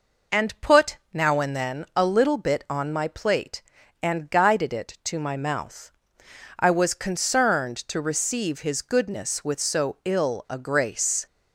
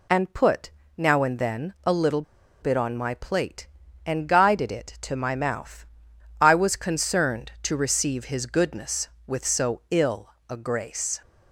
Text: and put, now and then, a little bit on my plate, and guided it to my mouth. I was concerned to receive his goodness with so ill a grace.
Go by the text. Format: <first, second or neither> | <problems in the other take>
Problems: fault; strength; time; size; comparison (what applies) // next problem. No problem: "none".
first | pauses between "little" and "bit"; at 2.2 s; 0.40 s long // pauses between "ill" and "a"; slight; at 10.3 s; 0.18 s long